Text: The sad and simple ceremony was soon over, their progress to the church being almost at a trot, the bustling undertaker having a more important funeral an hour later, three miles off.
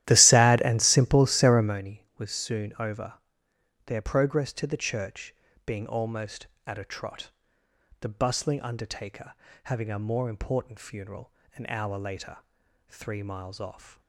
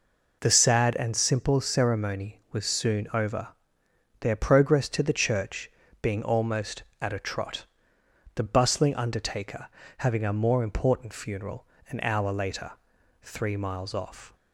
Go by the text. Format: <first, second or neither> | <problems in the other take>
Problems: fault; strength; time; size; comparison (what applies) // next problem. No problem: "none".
second | starts louder than the rest; strong; until 1.8 s; 14 dB // pauses between "church" and "being"; slight; at 5.3 s; 0.32 s long; slight in the second // pauses between "undertaker" and "having"; slight; at 9.3 s; 0.32 s long; slight in the second // pauses between "funeral" and "an"; slight; at 11.3 s; 0.24 s long; slight in the second